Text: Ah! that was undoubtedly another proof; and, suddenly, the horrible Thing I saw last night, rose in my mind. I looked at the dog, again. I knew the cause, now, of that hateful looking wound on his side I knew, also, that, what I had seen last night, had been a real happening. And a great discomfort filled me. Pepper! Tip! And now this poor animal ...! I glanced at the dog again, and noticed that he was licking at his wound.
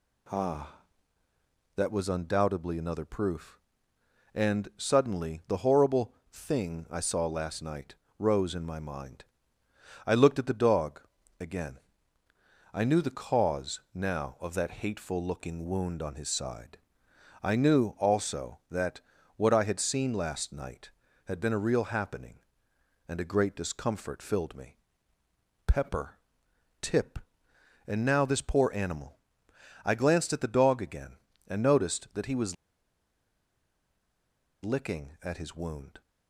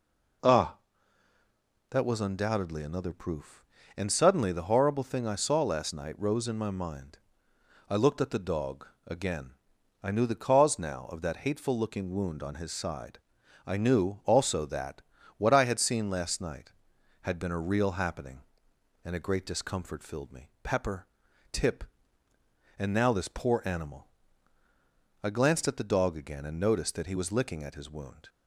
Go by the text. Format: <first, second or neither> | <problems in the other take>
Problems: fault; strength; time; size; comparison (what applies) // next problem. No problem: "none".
second | pauses between "horrible" and "Thing"; slight; at 6.1 s; 0.16 s long // pauses between "side" and "I"; noticeable; at 16.7 s; 0.64 s long; noticeable in the second // pauses between "was" and "licking"; strong; at 32.5 s; 2.0 s long